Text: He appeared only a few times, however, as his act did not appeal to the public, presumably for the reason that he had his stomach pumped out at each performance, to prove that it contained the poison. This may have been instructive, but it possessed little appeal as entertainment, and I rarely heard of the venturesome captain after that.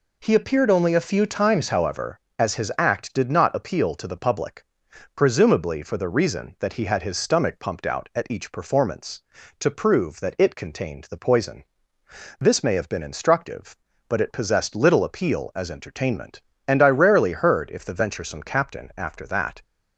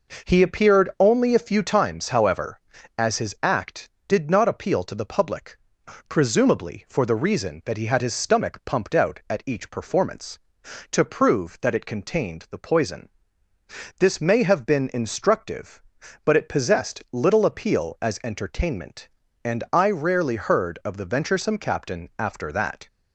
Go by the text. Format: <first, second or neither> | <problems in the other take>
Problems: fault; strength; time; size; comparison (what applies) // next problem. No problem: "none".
second | says "if" for "of"; at 17.7 s